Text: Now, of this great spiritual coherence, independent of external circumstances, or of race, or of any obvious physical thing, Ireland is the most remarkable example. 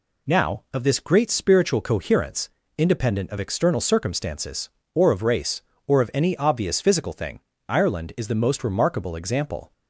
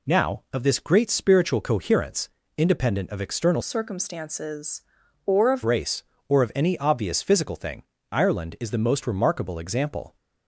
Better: first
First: none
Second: changes voice from "circumstances" to "of"; from 3.6 to 5.6 s; 2.0 s long

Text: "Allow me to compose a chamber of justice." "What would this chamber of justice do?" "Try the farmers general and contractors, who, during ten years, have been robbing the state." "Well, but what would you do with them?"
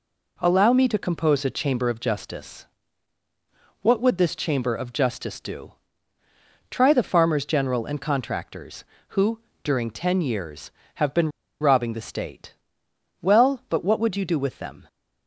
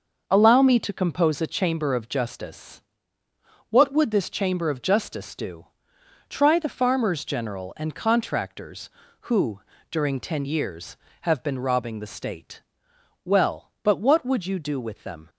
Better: second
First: pauses between "been" and "robbing"; slight; at 11.3 s; 0.30 s long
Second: none

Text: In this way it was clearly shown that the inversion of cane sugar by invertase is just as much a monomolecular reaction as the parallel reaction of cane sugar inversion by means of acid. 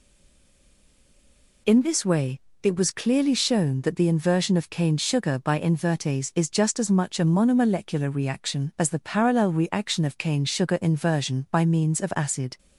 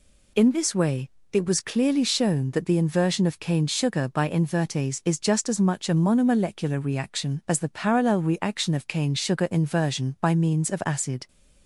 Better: second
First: stays silent before the first word; noticeable; until 1.6 s; 1.6 s long // pauses between "way" and "it"; slight; at 2.3 s; 0.22 s long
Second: pauses between "way" and "it"; slight; at 1.0 s; 0.22 s long

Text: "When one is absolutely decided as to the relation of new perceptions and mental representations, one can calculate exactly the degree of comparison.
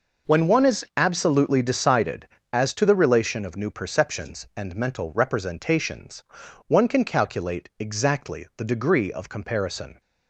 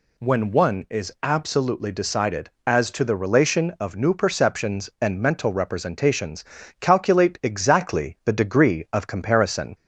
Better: first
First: none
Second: skips "one can"; at 6.6 s

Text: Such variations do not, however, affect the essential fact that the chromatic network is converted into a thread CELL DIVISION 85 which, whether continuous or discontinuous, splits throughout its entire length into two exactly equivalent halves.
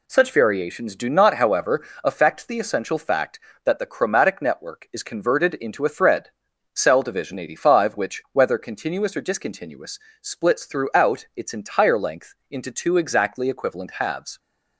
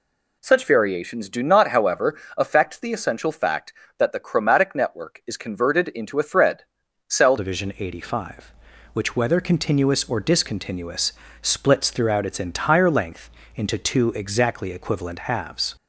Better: first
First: pauses between "thread" and "CELL"; at 6.3 s; 0.44 s long // pauses between "length" and "into"; slight; at 12.3 s; 0.16 s long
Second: pauses between "thread" and "CELL"; at 6.6 s; 0.44 s long // changes voice at "DIVISION"; from 7.3 s on; 8.4 s long // pauses between "length" and "into"; slight; at 13.2 s; 0.26 s long

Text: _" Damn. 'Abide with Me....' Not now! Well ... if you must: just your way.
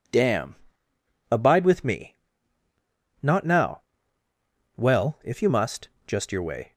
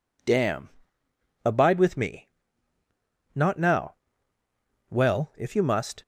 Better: first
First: none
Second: stops before "just your way"; at 6.0 s

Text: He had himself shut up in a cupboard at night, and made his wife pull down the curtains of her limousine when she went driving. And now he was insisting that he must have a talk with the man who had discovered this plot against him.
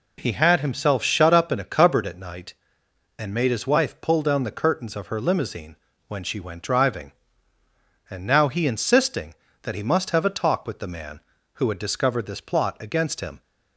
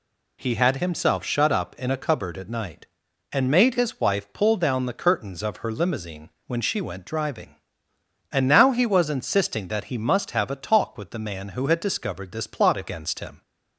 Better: second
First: pauses between "limousine" and "when"; slight; at 5.7 s; 0.32 s long // skips "was"; at 8.6 s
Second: pauses between "limousine" and "when"; slight; at 6.2 s; 0.18 s long

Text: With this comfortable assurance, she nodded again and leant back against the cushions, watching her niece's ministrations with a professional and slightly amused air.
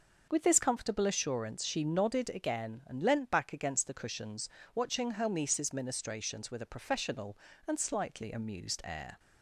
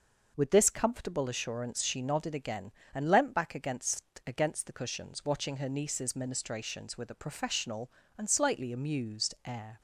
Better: first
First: none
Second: says "against" twice; at 4.2 s

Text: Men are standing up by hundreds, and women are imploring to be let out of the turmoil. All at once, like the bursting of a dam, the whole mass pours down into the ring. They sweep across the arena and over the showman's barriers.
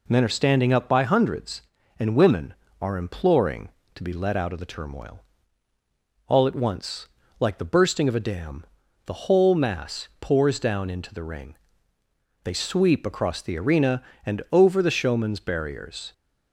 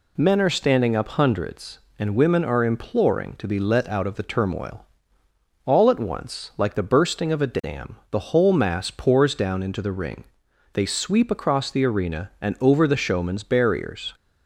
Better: first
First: none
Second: skips "by"; at 1.0 s

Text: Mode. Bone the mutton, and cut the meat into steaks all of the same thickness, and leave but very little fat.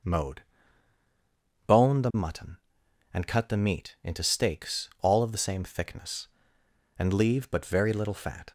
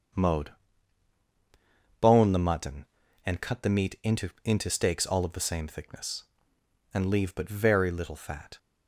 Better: first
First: none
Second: starts louder than the rest; until 2.6 s; 7 dB // says "into" twice; at 4.4 s

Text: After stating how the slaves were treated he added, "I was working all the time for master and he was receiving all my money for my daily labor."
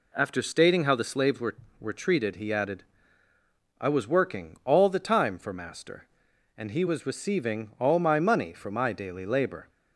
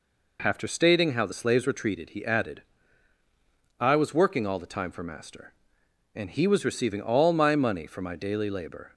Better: second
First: says "were" twice; at 1.8 s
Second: none

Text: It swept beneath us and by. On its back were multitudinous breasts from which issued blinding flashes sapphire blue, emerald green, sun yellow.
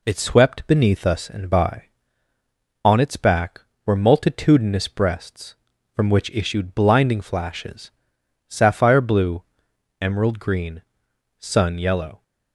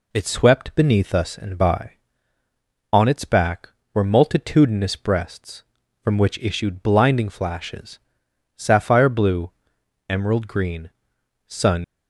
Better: first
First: pauses between "flashes" and "sapphire"; noticeable; at 7.9 s; 0.58 s long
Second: pauses between "flashes" and "sapphire"; noticeable; at 7.9 s; 0.58 s long // stops before "yellow"; at 11.8 s

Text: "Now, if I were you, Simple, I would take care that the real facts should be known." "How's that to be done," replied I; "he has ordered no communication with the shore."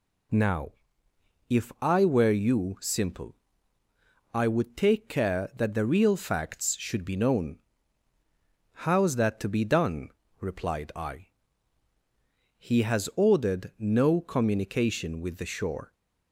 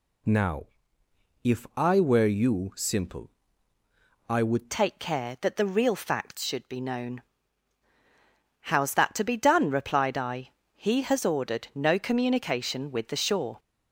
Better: first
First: none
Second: changes voice at "take"; from 4.7 s on; 8.8 s long

